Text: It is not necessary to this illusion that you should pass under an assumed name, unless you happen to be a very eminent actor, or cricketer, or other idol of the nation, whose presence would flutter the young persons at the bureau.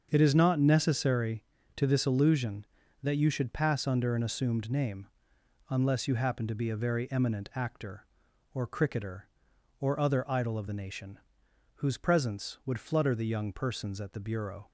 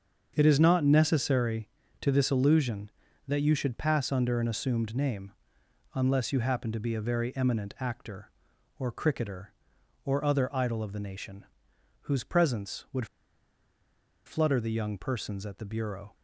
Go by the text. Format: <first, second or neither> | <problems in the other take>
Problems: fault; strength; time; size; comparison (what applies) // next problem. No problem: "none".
first | starts louder than the rest; until 1.3 s; 7 dB; also in the first // pauses between "would" and "flutter"; at 13.0 s; 1.1 s long